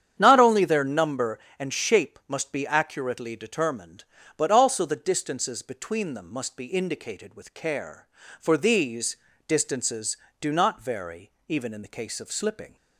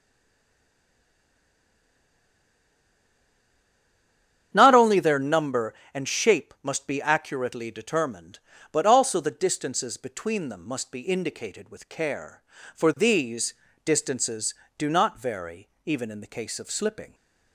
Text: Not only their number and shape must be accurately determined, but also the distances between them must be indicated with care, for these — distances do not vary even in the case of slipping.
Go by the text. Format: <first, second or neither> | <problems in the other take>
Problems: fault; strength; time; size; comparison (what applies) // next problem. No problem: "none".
first | stays silent before the first word; strong; until 4.5 s; 4.5 s long // starts louder than the rest; strong; until 5.5 s; 9 dB; strong in the first // pauses between "vary" and "even"; slight; at 15.6 s; 0.18 s long; slight in the first